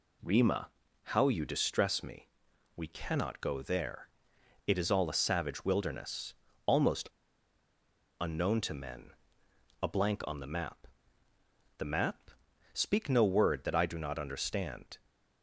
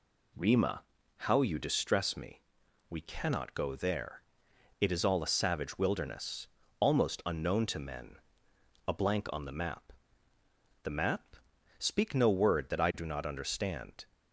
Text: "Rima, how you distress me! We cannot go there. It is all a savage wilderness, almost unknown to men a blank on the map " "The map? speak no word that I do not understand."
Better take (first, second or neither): second